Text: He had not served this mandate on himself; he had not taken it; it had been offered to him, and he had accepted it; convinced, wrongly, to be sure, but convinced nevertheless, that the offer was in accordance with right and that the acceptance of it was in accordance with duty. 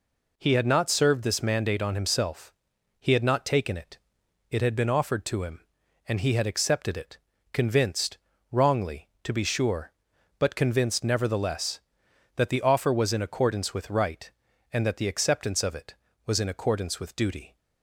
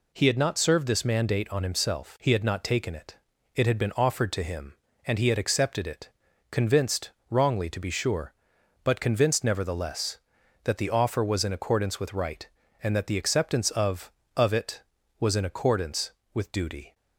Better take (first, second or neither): first